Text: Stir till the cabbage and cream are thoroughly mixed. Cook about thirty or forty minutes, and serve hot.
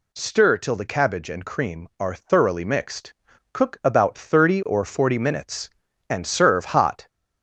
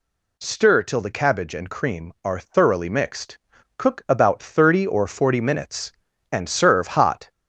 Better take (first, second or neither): neither